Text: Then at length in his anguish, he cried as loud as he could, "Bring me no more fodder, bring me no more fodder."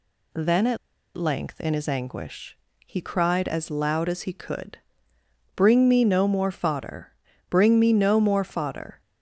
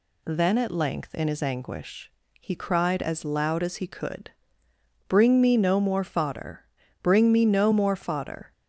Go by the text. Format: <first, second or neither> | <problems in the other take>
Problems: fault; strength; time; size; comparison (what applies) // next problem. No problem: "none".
second | pauses between "at" and "length"; at 0.7 s; 0.38 s long